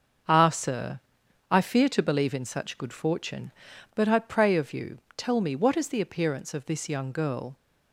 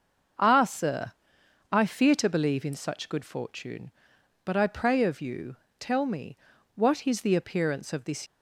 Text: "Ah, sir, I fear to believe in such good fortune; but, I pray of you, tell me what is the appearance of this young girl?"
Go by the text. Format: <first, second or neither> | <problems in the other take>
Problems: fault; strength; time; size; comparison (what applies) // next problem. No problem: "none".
first | starts louder than the rest; until 1.9 s; 6 dB; also in the first // pauses between "me" and "what"; at 6.3 s; 0.38 s long // stops before "young girl"; at 8.2 s